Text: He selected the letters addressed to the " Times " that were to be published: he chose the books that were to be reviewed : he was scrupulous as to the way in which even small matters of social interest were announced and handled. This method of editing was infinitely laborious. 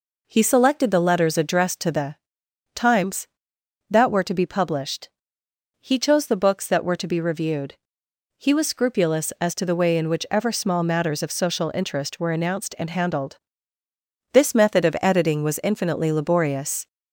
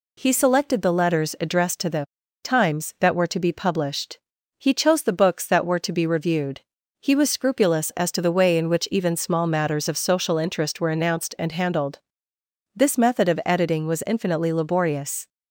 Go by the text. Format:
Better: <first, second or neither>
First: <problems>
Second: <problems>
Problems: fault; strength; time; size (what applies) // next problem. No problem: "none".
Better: second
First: says "ever" for "even"; at 10.3 s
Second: none